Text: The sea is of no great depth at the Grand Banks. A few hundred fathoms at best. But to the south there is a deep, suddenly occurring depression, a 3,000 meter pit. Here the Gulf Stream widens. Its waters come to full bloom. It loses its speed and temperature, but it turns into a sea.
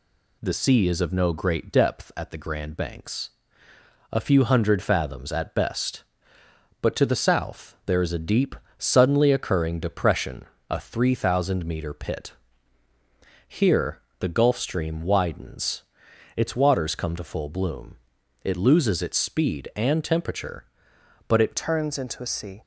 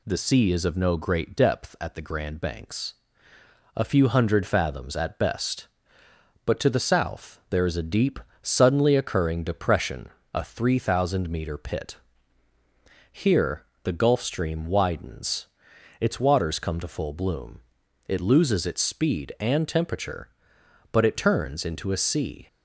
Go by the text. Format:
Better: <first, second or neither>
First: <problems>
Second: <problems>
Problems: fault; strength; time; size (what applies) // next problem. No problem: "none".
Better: second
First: pauses between "Here" and "the"; slight; at 13.9 s; 0.22 s long // changes voice at "turns"; from 21.5 s on; 1.1 s long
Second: pauses between "Here" and "the"; slight; at 13.6 s; 0.22 s long